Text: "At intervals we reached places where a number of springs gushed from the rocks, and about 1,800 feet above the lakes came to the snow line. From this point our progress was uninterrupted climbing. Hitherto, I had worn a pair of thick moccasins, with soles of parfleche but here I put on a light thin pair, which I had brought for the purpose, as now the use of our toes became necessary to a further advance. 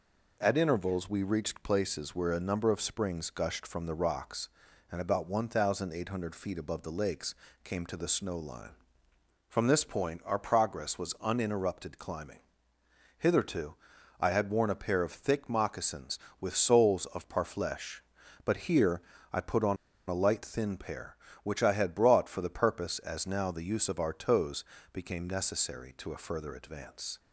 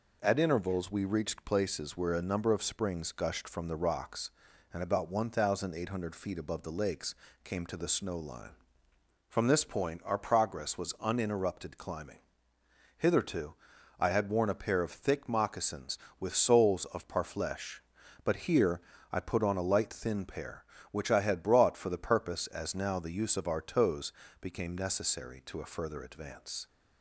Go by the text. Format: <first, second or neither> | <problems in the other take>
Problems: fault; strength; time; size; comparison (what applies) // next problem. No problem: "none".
second | pauses between "lakes" and "came"; slight; at 7.3 s; 0.26 s long; slight in the second // pauses between "here" and "I"; slight; at 18.9 s; 0.32 s long; slight in the second // pauses between "on" and "a"; slight; at 19.7 s; 0.32 s long // pauses between "toes" and "became"; slight; at 24.6 s; 0.28 s long; slight in the second